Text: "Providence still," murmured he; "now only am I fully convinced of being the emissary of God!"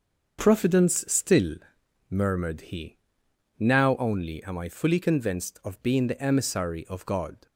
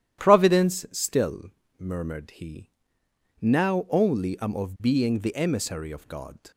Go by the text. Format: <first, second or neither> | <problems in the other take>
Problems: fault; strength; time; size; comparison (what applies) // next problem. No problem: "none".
first | starts louder than the rest; strong; until 1.2 s; 11.5 dB; also in the first // skips "I fully convinced"; at 4.5 s